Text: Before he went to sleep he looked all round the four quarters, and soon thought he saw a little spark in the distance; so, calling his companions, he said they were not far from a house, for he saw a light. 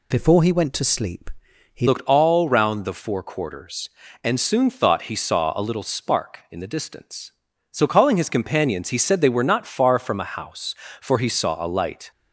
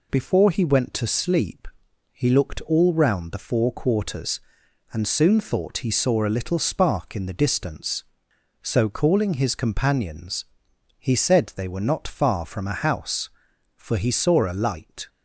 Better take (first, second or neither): second